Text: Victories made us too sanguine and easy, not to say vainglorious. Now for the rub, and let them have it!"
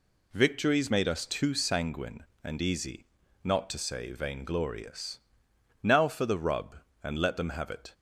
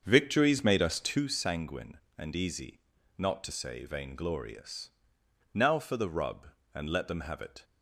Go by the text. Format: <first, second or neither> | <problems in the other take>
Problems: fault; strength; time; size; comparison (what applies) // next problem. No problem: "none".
first | starts louder than the rest; until 1.3 s; 7 dB